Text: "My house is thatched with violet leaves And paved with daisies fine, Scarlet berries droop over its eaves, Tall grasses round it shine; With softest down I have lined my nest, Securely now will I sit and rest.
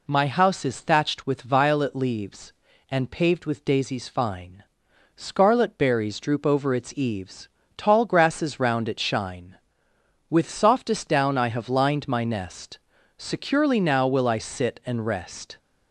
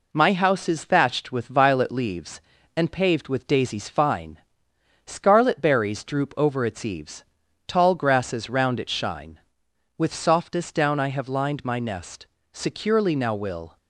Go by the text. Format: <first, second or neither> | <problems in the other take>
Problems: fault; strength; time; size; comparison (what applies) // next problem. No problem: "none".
first | stops before "I sit and rest"; at 13.7 s